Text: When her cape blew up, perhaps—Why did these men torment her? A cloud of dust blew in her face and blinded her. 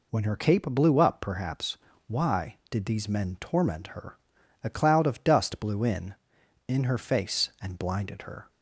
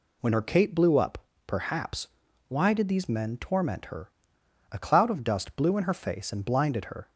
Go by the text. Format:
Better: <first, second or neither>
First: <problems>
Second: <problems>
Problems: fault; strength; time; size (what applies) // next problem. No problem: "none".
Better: second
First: says "in" twice; at 6.6 s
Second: none